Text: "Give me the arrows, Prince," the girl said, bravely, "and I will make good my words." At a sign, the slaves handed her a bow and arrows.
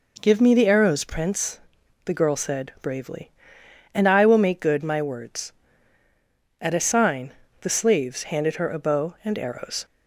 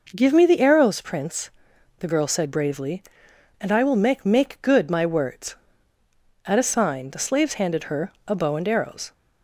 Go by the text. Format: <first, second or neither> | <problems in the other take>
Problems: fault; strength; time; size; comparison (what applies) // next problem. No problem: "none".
first | says "make" twice; at 4.2 s